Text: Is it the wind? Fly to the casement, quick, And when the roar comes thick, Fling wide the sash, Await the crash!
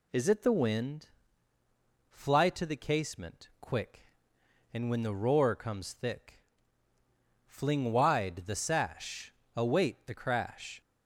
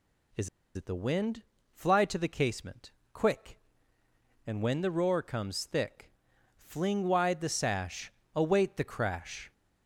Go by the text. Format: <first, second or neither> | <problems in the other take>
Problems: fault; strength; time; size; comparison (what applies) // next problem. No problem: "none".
first | pauses between "Is" and "it"; slight; at 0.4 s; 0.27 s long